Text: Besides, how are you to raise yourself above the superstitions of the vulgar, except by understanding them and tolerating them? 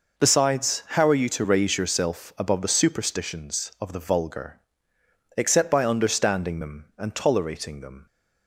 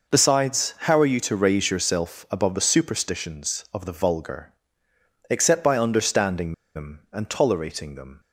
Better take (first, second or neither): first